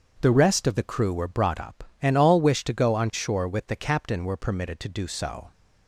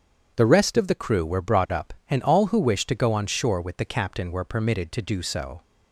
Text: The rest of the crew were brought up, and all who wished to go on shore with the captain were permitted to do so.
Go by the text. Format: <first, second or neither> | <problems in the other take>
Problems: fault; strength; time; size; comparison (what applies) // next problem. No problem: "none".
second | starts louder than the rest; strong; until 1.2 s; 7.5 dB; strong in the second // skips "who"; at 2.4 s